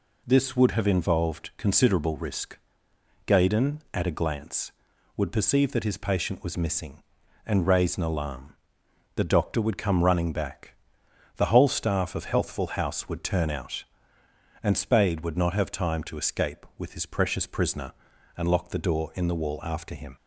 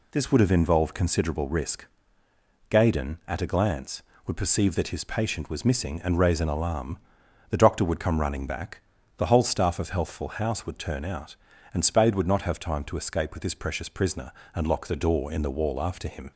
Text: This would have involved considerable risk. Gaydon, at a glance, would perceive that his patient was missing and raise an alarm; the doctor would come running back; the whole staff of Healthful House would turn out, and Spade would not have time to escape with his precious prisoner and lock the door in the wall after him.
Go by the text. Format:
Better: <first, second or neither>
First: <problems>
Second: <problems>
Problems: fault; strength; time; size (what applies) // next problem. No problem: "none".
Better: neither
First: none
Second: none